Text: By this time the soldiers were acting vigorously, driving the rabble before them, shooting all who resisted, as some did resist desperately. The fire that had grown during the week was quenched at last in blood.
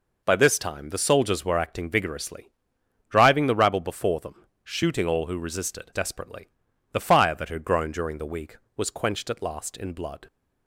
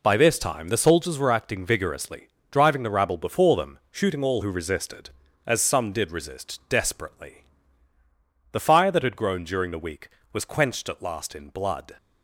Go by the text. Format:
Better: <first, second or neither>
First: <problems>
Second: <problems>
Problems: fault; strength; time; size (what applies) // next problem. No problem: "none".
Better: second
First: skips "as some did resist"; at 5.9 s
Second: none